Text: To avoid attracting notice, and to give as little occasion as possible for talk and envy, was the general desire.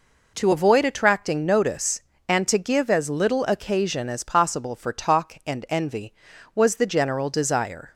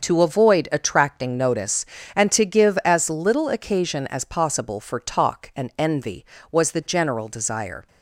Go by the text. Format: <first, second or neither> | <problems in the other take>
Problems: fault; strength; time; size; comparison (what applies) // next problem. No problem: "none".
first | loses the start of "To"; at 0.0 s; 35 ms // starts louder than the rest; until 1.0 s; 6.5 dB